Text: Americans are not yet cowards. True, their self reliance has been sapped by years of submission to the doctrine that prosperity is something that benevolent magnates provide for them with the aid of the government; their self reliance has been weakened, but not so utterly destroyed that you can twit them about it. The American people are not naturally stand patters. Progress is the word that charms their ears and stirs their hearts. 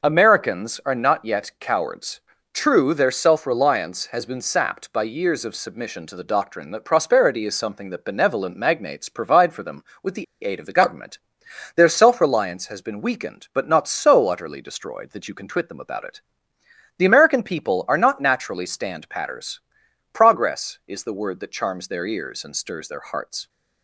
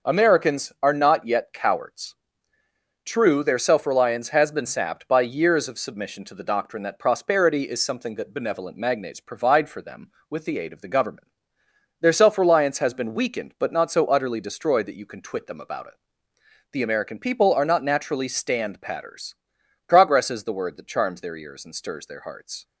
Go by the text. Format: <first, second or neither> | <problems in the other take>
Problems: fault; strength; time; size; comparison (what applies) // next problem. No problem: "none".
second | starts louder than the rest; until 1.1 s; 6 dB; noticeable in the second // pauses between "the" and "aid"; slight; at 10.2 s; 0.19 s long